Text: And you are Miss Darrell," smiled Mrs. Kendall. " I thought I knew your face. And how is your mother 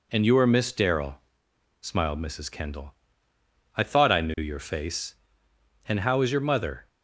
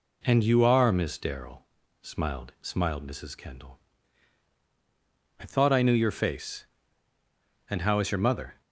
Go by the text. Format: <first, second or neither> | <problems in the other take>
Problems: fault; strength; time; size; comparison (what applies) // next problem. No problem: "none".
first | says "smiled" twice; at 2.6 s